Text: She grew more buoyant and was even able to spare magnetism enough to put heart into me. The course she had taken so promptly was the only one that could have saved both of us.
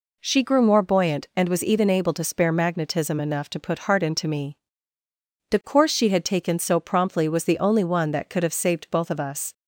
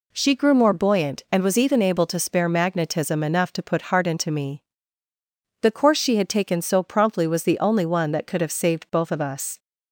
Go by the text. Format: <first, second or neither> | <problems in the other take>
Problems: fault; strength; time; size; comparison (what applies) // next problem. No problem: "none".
neither | none